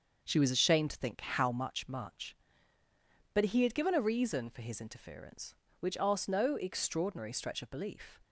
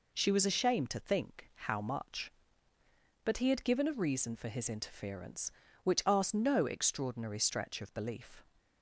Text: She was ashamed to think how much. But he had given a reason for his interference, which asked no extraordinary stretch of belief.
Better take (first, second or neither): second